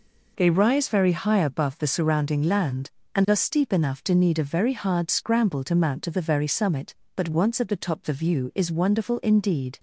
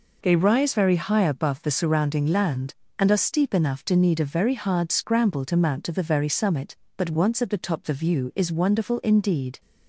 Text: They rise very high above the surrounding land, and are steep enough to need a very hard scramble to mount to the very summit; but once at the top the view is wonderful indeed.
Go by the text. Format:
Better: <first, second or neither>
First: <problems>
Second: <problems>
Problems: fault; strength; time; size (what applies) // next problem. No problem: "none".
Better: neither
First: none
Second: none